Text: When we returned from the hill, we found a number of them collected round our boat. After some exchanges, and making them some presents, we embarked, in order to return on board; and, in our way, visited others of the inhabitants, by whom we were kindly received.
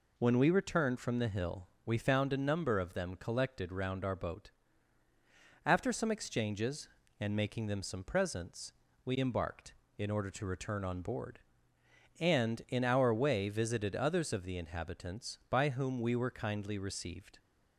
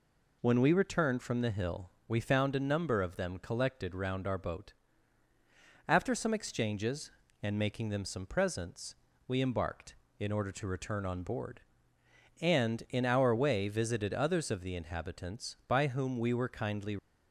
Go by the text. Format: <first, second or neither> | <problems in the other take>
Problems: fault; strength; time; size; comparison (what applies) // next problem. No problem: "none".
first | stops before "received"; at 16.9 s